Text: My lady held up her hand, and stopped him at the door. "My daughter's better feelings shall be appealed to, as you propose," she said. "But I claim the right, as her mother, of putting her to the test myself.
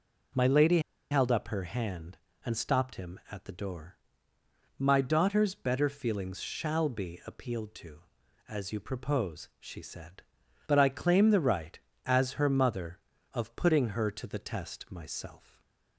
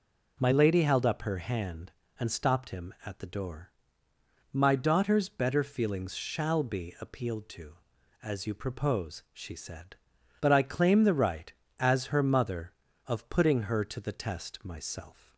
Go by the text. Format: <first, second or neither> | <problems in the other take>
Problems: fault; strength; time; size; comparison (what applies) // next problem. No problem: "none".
second | pauses between "lady" and "held"; slight; at 0.7 s; 0.31 s long